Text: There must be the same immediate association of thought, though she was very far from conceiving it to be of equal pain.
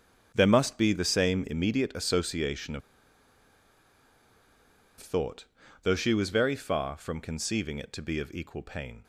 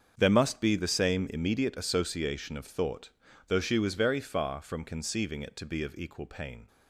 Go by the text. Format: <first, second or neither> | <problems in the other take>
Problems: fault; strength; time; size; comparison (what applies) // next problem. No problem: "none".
second | starts louder than the rest; strong; until 1.3 s; 7.5 dB; strong in the second // pauses between "of" and "thought"; strong; at 2.8 s; 2.1 s long